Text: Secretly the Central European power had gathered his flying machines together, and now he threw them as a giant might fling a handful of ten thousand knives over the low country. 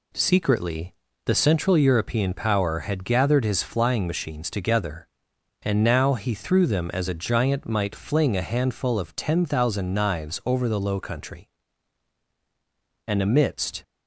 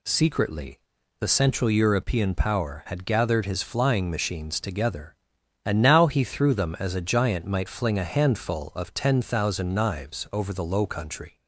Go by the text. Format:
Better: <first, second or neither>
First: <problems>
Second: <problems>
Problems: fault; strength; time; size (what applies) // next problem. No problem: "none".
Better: second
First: pauses between "Secretly" and "the"; slight; at 0.9 s; 0.30 s long // goes on to say "And amidst"; noticeable; from 13.0 s on; 0.76 s long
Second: pauses between "Secretly" and "the"; at 0.7 s; 0.40 s long